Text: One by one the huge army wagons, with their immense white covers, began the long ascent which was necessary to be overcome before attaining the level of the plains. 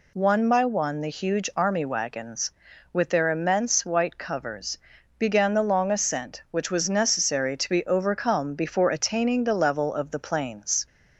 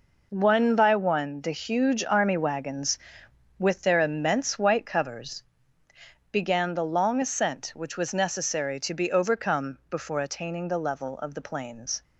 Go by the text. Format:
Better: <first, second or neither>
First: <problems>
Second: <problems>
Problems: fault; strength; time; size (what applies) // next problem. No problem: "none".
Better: first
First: none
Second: gets quieter; strong; throughout; 9 dB